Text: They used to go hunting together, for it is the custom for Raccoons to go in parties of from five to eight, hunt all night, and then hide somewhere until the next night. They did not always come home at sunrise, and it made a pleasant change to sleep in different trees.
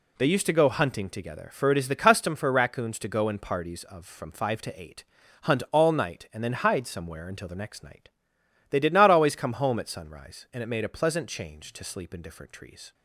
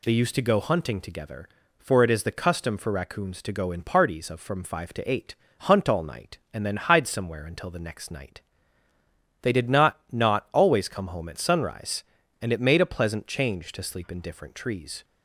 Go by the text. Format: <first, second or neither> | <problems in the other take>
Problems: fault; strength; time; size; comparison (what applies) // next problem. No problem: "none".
first | says "not" twice; at 10.1 s